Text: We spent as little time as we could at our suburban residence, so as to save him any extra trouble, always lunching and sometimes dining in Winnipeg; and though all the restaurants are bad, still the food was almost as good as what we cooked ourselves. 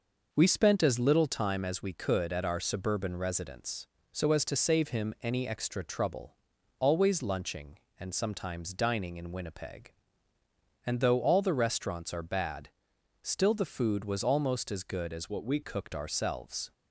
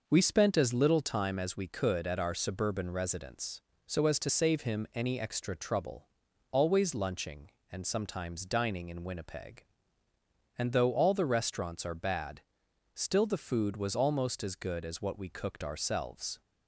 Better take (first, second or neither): second